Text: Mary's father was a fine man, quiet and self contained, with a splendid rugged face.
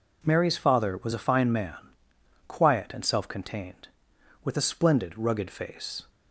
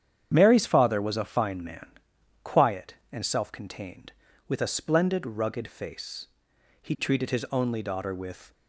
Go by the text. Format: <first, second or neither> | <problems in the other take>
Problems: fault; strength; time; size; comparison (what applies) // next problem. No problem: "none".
first | starts louder than the rest; strong; until 1.3 s; 8.5 dB // goes on to say "He treated his only daughter with"; strong; from 6.8 s on; 1.7 s long